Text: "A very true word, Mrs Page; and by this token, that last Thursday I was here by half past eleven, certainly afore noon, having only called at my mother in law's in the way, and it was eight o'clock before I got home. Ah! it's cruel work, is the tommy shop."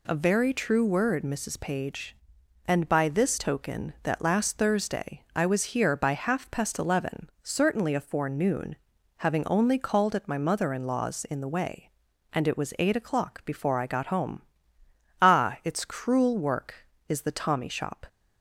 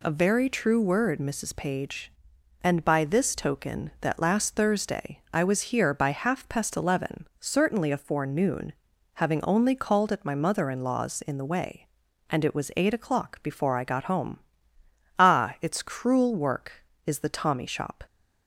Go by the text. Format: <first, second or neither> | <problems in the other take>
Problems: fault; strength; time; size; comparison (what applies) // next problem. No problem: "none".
neither | none